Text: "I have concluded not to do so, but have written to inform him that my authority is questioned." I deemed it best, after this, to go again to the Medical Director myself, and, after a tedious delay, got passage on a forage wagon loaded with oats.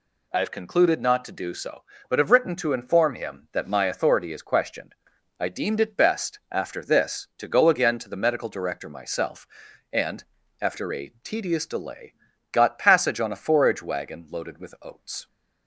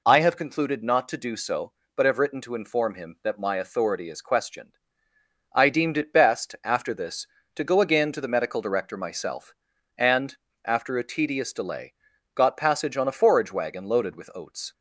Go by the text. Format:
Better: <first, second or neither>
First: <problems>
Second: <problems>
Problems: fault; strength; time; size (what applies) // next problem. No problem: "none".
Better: neither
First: none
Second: none